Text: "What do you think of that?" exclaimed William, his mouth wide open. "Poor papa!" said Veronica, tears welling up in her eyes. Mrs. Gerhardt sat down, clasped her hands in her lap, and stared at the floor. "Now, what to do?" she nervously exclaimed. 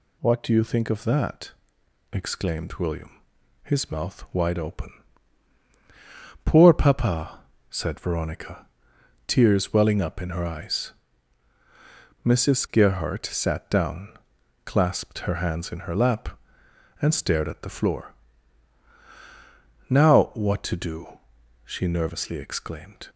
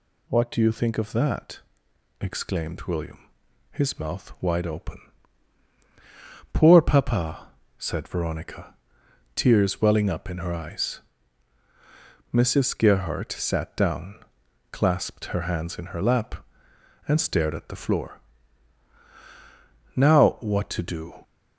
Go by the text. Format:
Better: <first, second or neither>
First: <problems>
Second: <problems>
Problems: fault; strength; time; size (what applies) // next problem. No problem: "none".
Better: first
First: none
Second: stops before "she nervously exclaimed"; at 21.2 s